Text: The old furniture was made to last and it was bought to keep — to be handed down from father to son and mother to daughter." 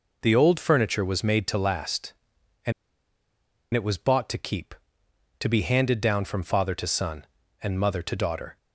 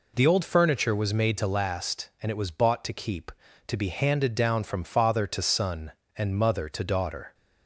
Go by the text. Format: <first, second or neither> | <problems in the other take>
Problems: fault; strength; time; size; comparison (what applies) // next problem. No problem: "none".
second | pauses between "and" and "it"; at 2.7 s; 1.0 s long